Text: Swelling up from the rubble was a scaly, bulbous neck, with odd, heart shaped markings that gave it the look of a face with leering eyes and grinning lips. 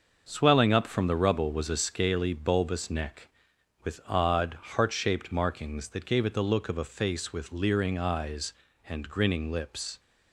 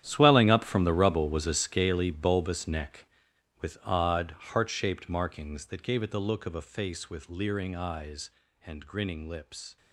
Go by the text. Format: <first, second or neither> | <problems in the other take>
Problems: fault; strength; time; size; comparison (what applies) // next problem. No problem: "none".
first | gets quieter; strong; throughout; 15.5 dB // starts louder than the rest; strong; until 1.0 s; 11 dB; also in the first